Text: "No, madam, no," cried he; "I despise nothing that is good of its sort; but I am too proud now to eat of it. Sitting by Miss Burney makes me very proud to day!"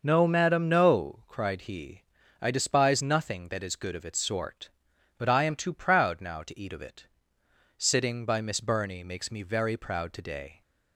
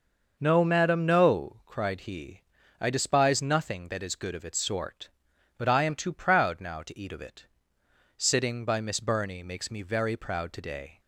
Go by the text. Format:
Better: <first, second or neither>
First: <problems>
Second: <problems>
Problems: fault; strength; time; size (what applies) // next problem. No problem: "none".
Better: neither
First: none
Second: none